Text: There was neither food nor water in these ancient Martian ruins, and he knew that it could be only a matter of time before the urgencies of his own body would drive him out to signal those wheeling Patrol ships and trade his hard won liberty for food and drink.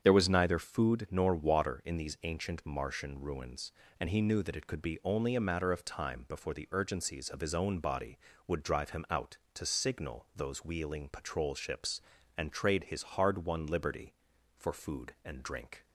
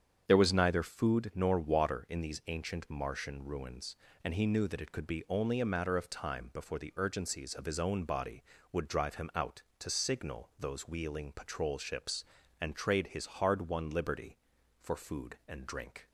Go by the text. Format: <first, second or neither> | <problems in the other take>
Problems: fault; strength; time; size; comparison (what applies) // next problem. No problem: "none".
neither | starts louder than the rest; strong; the same in both